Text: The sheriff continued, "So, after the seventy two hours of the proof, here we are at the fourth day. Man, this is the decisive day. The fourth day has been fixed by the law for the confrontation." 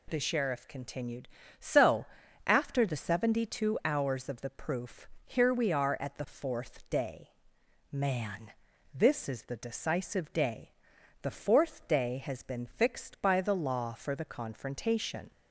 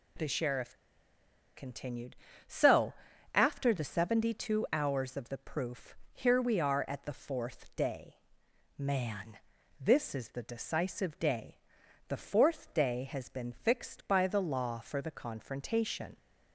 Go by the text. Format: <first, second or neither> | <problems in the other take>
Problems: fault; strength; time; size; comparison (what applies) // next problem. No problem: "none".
first | pauses between "sheriff" and "continued"; noticeable; at 0.7 s; 0.80 s long